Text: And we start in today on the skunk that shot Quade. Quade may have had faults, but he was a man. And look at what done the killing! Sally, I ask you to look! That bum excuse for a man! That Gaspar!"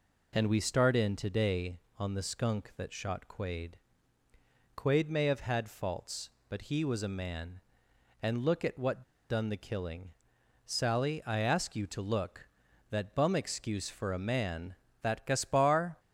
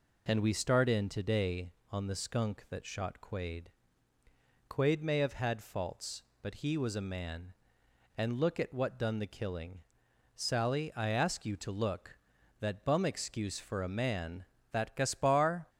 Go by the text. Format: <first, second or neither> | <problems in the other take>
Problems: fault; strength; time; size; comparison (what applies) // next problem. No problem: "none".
second | pauses between "what" and "done"; slight; at 9.0 s; 0.25 s long